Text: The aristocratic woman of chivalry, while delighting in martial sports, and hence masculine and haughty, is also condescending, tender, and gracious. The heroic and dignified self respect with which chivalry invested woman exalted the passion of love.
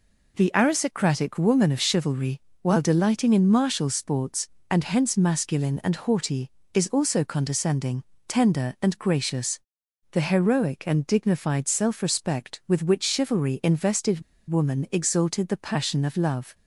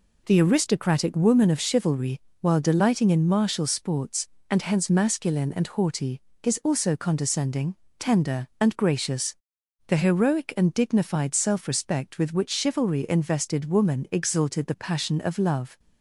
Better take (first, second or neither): second